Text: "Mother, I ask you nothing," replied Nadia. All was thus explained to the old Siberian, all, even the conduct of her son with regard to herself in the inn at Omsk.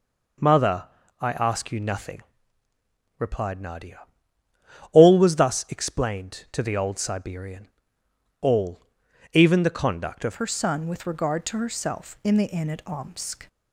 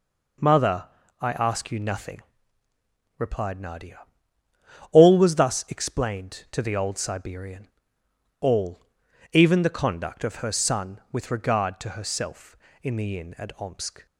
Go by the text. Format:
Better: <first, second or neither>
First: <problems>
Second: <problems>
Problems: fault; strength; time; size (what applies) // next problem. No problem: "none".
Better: second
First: changes voice at "her"; from 10.3 s on; 3.1 s long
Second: none